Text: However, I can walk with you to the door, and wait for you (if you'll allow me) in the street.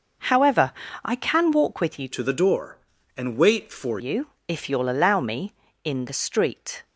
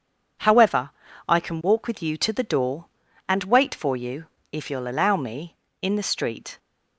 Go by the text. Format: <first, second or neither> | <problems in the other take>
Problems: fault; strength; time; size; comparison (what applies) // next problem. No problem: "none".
second | changes voice from "to" to "for"; from 2.1 to 3.9 s; 1.8 s long